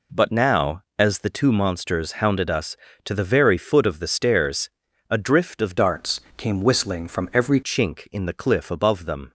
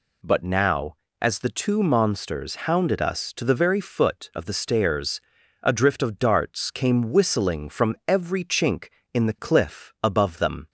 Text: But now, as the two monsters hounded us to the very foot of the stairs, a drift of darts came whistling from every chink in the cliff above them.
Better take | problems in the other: second | changes voice from "darts" to "every"; from 5.7 to 7.6 s; 1.9 s long // pauses between "darts" and "came"; slight; at 6.2 s; 0.16 s long

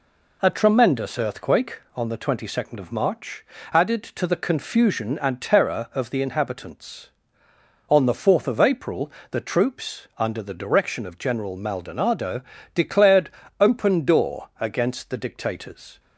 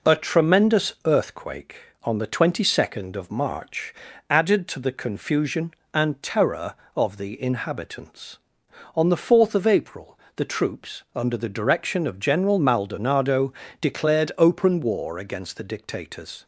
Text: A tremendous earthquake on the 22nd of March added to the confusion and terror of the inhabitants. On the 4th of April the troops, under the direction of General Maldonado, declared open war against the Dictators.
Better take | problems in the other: second | pauses between "March" and "added"; slight; at 3.4 s; 0.26 s long; slight in the second // pauses between "April" and "the"; slight; at 9.0 s; 0.20 s long; slight in the second // pauses between "declared" and "open"; slight; at 13.2 s; 0.32 s long // says "door" for "war"; at 14.0 s

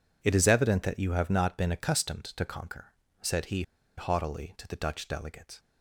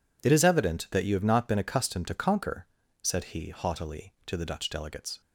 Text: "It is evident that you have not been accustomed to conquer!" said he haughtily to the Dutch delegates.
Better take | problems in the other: second | pauses between "he" and "haughtily"; slight; at 3.6 s; 0.34 s long

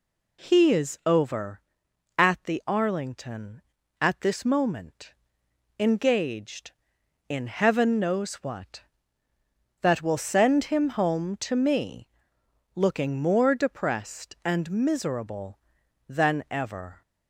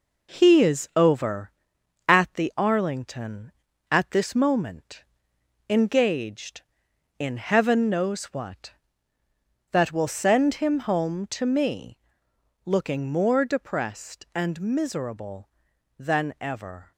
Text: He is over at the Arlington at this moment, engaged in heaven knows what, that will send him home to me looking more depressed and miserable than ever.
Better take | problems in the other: first | gets quieter; noticeable; throughout; 6 dB // pauses between "me" and "looking"; noticeable; at 11.9 s; 0.66 s long; noticeable in the first

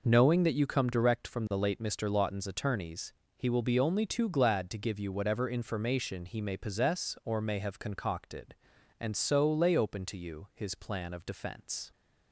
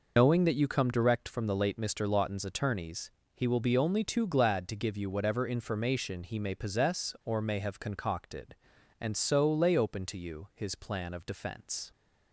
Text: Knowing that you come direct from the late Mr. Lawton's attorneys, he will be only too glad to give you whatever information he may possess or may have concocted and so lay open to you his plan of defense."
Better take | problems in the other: first | loses the start of "Knowing"; at 0.1 s; 115 ms

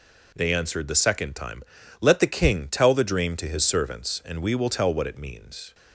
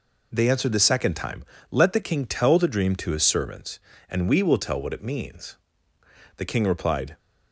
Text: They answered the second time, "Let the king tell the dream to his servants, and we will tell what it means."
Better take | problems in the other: first | goes on to say "The king replied"; noticeable; from 6.3 s on; 0.80 s long

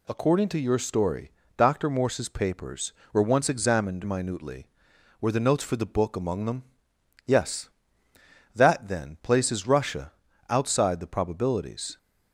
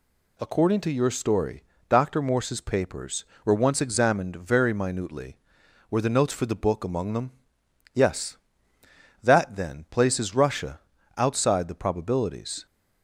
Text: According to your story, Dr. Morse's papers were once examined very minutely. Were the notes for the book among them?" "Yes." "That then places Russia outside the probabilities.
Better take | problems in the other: second | skips "very"; at 4.0 s // pauses between "Russia" and "outside"; slight; at 10.1 s; 0.34 s long; slight in the second

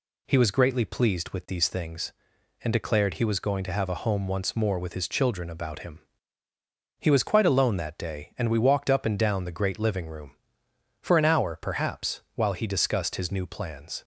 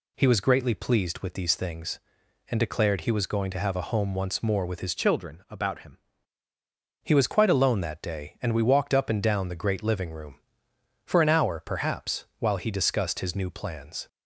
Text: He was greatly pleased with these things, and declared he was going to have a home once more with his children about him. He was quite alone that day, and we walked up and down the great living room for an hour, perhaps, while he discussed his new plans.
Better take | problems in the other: first | changes voice from "children" to "him"; from 4.9 to 5.9 s; 1.0 s long

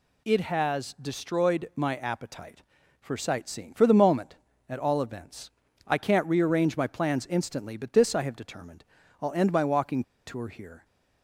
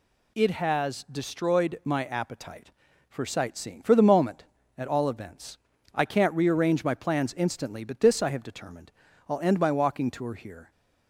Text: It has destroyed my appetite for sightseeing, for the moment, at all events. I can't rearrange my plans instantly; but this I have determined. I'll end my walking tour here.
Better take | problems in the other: second | pauses between "walking" and "tour"; slight; at 10.0 s; 0.22 s long

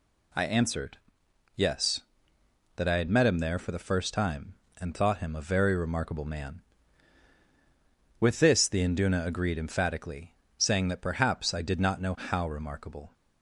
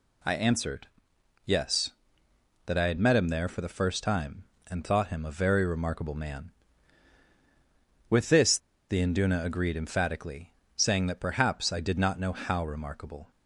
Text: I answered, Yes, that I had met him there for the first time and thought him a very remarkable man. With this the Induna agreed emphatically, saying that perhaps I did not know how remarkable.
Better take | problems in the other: first | pauses between "this" and "the"; slight; at 8.5 s; 0.31 s long

